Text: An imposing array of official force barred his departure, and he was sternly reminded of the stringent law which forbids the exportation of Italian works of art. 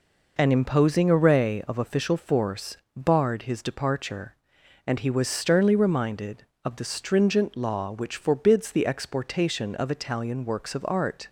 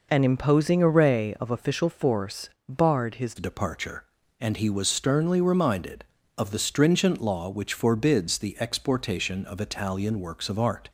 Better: first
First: pauses between "force" and "barred"; slight; at 2.7 s; 0.18 s long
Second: pauses between "force" and "barred"; slight; at 2.4 s; 0.18 s long // changes voice at "departure"; from 3.3 s on; 7.5 s long

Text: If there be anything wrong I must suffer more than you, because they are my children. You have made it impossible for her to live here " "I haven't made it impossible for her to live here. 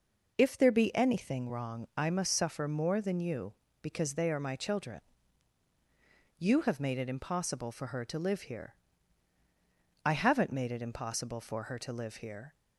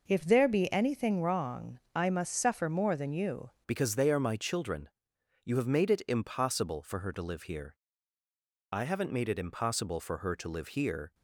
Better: first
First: none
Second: changes voice at "because"; from 3.6 s on; 7.5 s long

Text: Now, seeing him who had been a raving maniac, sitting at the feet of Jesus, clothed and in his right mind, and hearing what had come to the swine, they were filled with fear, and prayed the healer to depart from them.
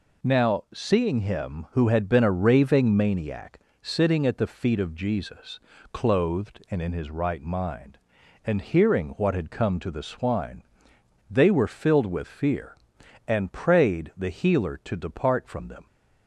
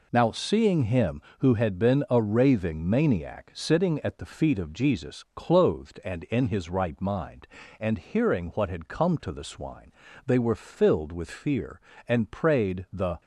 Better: first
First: none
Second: stops before "healer to depart from them"; at 13.2 s

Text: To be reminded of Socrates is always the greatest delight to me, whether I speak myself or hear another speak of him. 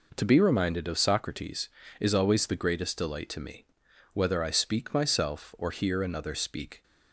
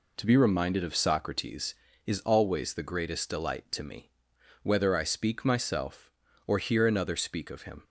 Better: second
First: stops before "of him"; at 6.8 s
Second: none

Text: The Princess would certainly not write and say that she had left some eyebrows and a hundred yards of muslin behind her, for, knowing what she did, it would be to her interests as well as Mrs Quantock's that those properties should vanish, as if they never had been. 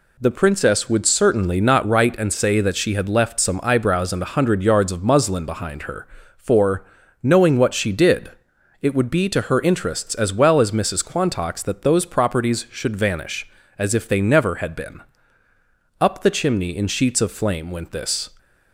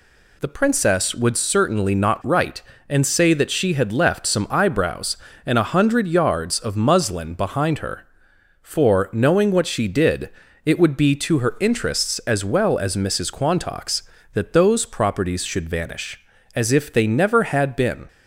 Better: second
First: goes on to say "Up the chimney in sheets of flame went this"; strong; from 16.0 s on; 2.3 s long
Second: none

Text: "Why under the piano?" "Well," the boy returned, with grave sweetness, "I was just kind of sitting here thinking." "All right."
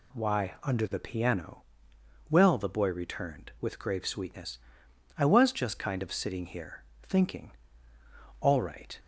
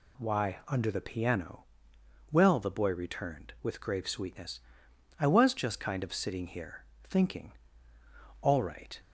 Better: neither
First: pauses between "here" and "thinking"; slight; at 6.8 s; 0.18 s long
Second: pauses between "here" and "thinking"; slight; at 6.8 s; 0.18 s long

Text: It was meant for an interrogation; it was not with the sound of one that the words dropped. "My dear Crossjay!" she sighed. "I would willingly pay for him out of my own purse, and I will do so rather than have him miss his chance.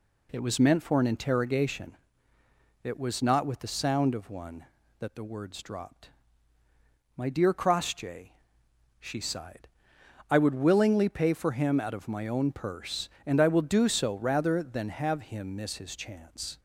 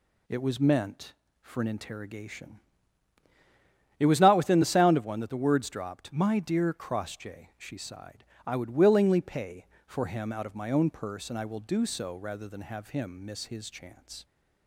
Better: first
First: none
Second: says "within" for "with"; at 4.3 s

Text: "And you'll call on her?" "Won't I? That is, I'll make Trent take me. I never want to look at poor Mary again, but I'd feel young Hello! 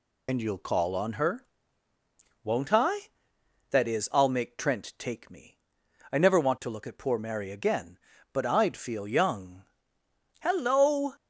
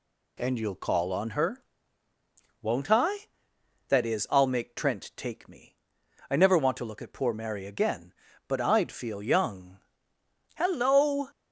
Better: second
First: loses the start of "And"; at 0.2 s; 85 ms // pauses between "young" and "Hello"; noticeable; at 9.6 s; 0.76 s long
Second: pauses between "young" and "Hello"; noticeable; at 9.7 s; 0.76 s long

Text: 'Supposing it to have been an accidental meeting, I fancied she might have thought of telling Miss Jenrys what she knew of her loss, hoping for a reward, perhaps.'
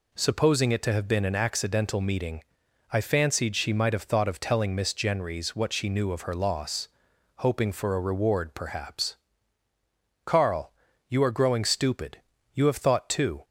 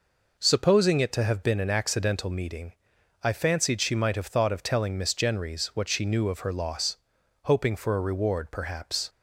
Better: second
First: goes on to say "Carl you are growing stupid You have thought too"; strong; from 10.2 s on; 3.2 s long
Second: none

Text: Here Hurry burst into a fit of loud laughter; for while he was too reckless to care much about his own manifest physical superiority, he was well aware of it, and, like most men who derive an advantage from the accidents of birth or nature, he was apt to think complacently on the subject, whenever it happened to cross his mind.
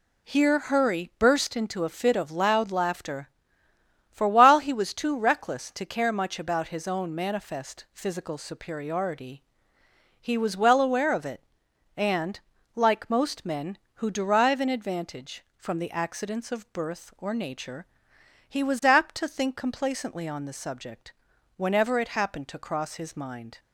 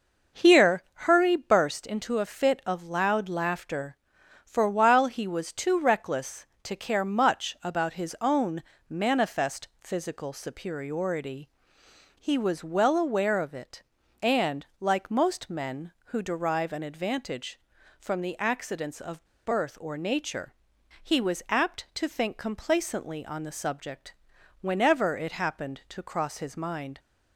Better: first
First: none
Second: starts louder than the rest; until 1.5 s; 6.5 dB // pauses between "Here" and "Hurry"; slight; at 0.8 s; 0.24 s long // pauses between "own" and "manifest"; slight; at 8.6 s; 0.26 s long // pauses between "of" and "birth"; slight; at 19.2 s; 0.20 s long

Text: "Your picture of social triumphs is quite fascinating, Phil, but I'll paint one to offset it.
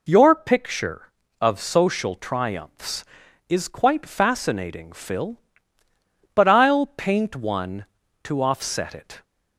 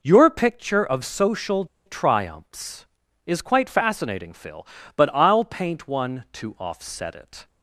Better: first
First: none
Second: pauses between "social" and "triumphs"; slight; at 1.6 s; 0.20 s long

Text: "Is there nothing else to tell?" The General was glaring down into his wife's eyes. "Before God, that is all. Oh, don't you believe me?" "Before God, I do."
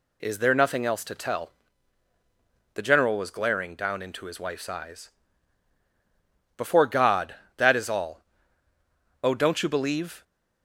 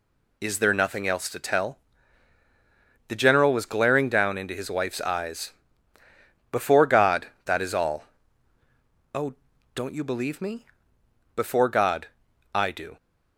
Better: second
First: stops before "me Before God I do"; at 10.2 s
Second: none

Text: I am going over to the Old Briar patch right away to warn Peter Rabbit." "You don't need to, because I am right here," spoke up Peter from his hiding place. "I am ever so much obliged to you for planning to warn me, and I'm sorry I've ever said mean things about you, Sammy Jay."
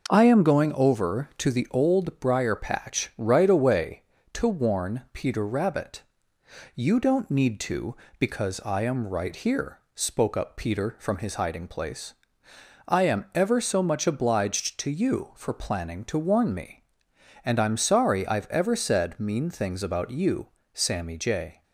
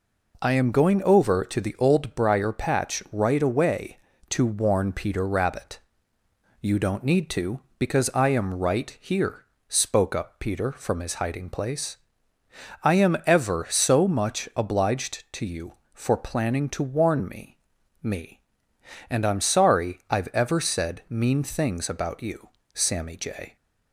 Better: first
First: none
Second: says "me" twice; at 18.0 s

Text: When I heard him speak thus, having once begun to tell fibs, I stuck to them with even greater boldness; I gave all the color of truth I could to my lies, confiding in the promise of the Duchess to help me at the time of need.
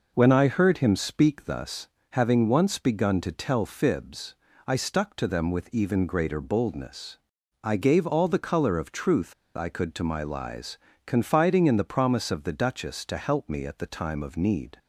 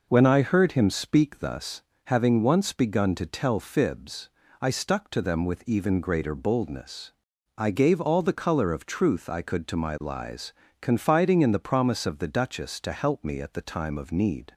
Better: second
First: pauses between "truth" and "I"; slight; at 9.3 s; 0.22 s long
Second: none

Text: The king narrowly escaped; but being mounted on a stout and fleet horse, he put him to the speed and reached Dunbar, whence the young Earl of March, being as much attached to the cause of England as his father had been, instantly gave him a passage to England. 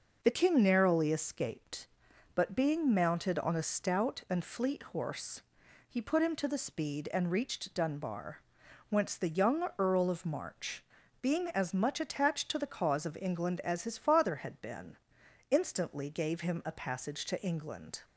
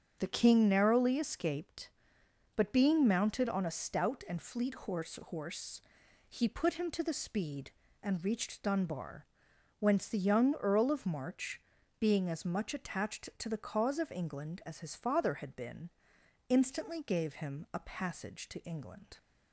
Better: first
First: none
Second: starts louder than the rest; strong; until 1.2 s; 7.5 dB // says "horse" twice; at 5.2 s

